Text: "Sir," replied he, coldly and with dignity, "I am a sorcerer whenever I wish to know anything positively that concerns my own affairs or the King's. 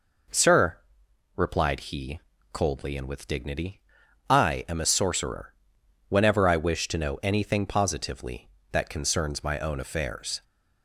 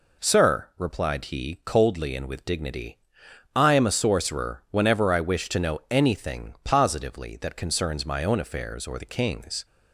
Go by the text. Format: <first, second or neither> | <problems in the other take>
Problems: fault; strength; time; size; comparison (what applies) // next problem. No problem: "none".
second | pauses between "sorcerer" and "whenever"; noticeable; at 5.5 s; 0.54 s long // stops before "or the King's"; at 10.4 s